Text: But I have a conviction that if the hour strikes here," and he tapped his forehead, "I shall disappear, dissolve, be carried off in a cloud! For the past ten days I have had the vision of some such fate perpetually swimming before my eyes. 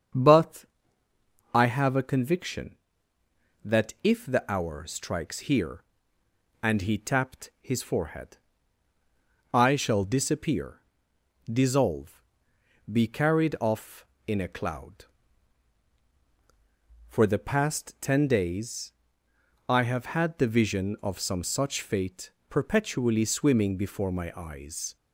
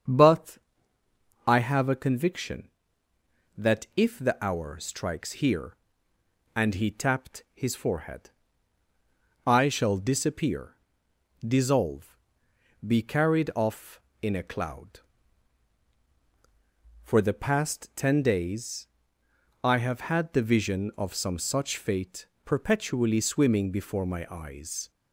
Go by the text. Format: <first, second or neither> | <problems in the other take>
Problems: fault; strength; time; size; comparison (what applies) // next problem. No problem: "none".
neither | starts louder than the rest; strong; the same in both // pauses between "But" and "I"; noticeable; the same in both // pauses between "days" and "I"; noticeable; the same in both // pauses between "fate" and "perpetually"; slight; the same in both